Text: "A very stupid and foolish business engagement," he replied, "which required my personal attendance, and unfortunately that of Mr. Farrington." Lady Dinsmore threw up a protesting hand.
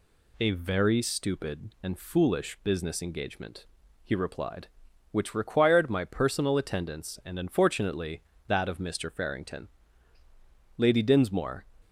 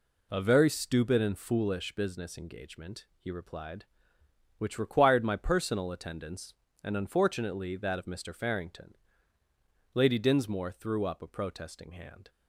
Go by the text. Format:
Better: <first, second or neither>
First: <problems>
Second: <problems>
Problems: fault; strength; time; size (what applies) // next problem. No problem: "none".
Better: second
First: stops before "threw up a protesting hand"; at 11.8 s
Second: none